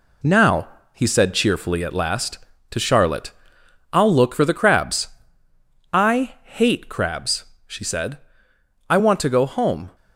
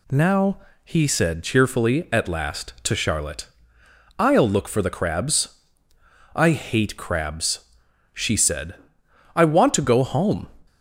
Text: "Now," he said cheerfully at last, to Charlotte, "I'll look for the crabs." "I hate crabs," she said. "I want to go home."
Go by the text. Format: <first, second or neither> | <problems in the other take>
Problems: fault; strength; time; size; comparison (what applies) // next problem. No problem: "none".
second | gets quieter; noticeable; throughout; 6 dB